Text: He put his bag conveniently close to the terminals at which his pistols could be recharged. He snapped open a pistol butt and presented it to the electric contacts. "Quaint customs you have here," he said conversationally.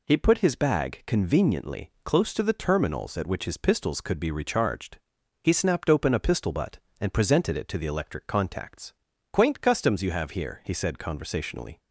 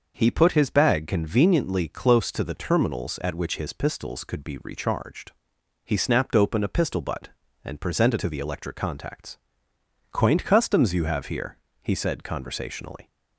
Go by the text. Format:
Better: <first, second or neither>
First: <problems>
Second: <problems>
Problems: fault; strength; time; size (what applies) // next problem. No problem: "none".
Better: first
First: none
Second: starts louder than the rest; noticeable; until 1.1 s; 6 dB // skips "it"; at 8.1 s